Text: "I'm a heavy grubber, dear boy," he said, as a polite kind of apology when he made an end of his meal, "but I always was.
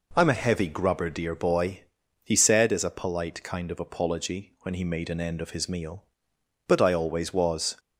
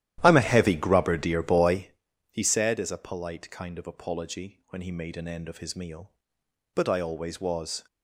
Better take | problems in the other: first | starts louder than the rest; strong; until 2.0 s; 12.5 dB

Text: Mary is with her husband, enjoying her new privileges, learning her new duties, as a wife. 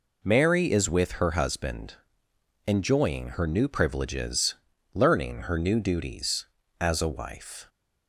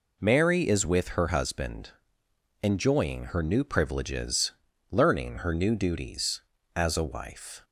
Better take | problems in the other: neither | none

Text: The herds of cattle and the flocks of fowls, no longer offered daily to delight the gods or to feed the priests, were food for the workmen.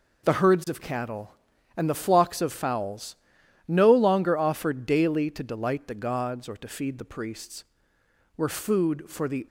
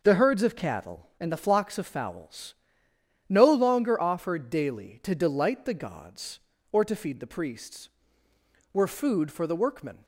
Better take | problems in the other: second | stops before "workmen"; at 9.4 s

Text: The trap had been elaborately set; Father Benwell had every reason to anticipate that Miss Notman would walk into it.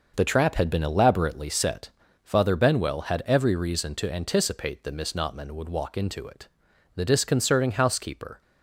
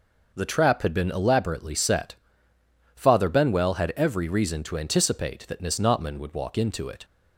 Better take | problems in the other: second | goes on to say "The disconcerting housekeeper"; from 6.9 s on; 1.4 s long

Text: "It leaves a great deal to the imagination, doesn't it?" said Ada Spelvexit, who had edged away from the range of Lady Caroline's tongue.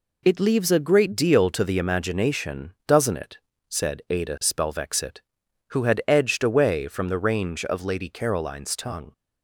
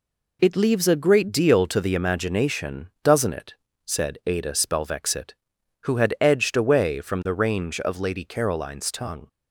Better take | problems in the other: neither | none

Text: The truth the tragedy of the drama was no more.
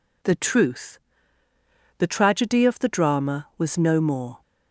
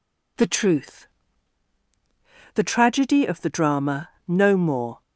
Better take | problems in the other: first | pauses between "truth" and "the"; strong; at 1.0 s; 1.4 s long; noticeable in the first // skips "was"; at 4.1 s

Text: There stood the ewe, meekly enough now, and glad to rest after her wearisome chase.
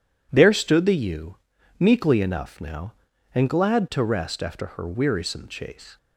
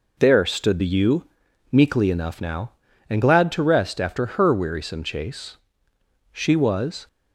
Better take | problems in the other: first | goes on to say "She was"; noticeable; from 6.3 s on; 0.76 s long

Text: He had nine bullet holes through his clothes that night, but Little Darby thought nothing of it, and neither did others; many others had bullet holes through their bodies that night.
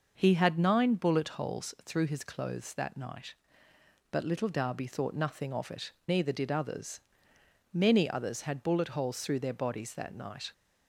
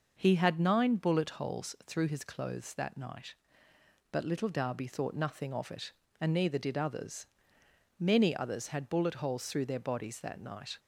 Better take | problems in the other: second | skips "and"; at 6.0 s

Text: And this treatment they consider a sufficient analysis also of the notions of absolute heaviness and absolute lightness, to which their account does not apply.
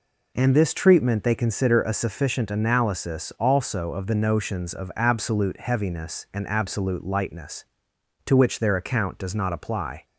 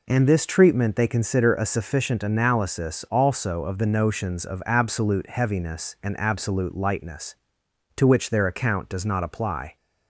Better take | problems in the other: neither | none

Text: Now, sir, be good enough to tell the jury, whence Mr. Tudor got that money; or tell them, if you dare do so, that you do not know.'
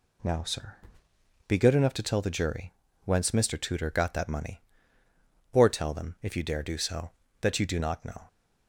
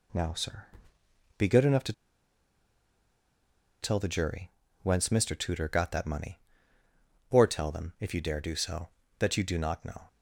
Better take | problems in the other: first | pauses between "to" and "tell"; strong; at 1.9 s; 1.9 s long

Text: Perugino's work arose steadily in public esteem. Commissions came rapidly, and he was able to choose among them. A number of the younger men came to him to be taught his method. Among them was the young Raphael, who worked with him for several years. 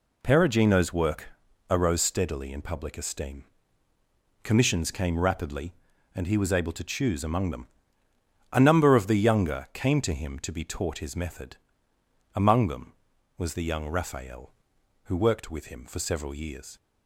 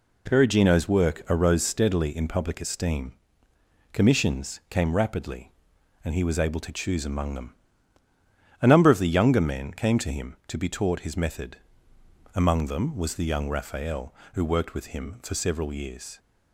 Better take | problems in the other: second | pauses between "work" and "arose"; at 1.2 s; 0.42 s long // skips "men"; at 9.6 s

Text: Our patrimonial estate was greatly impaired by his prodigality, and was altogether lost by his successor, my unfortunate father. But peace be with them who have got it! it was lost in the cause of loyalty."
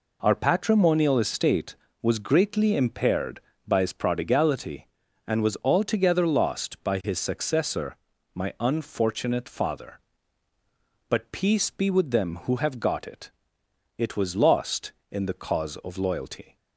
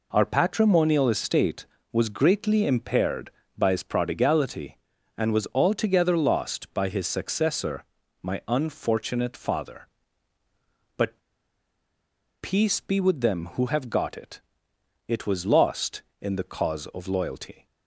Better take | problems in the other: first | pauses between "But" and "peace"; at 11.1 s; 1.2 s long

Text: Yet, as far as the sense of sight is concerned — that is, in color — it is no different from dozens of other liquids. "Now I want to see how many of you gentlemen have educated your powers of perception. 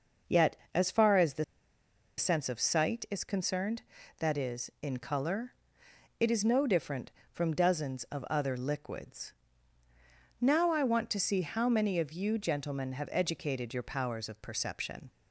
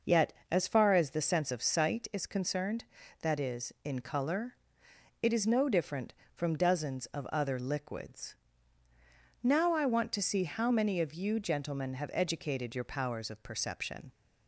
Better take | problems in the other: second | pauses between "the" and "sense"; noticeable; at 1.4 s; 0.73 s long

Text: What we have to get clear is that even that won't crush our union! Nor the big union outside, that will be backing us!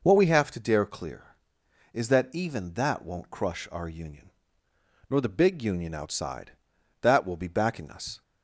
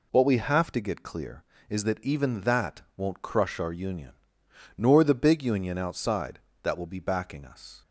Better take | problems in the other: second | says "dare" for "get"; at 0.6 s

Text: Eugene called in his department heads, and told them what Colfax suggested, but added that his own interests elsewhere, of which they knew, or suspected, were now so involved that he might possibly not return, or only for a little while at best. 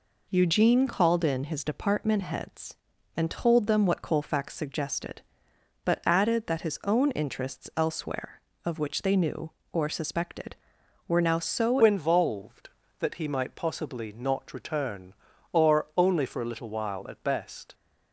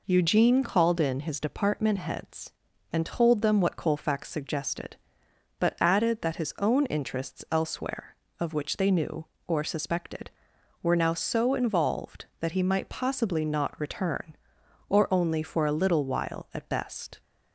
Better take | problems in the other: second | changes voice at "involved"; from 11.8 s on; 5.9 s long

